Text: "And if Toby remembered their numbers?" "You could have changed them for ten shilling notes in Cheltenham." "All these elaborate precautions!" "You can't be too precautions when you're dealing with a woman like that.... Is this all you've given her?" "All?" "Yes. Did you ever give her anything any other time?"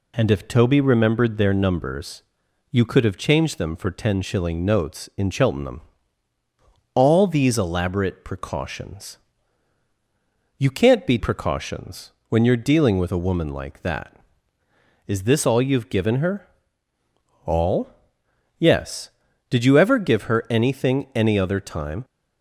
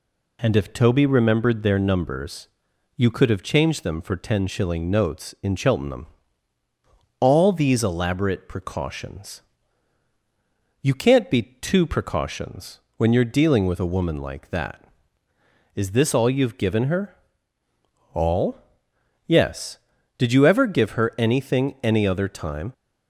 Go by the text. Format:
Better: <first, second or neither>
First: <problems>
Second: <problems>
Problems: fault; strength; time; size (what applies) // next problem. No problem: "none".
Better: second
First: skips "too"; at 11.1 s // pauses between "precautions" and "when"; slight; at 12.1 s; 0.18 s long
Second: pauses between "precautions" and "when"; slight; at 12.7 s; 0.18 s long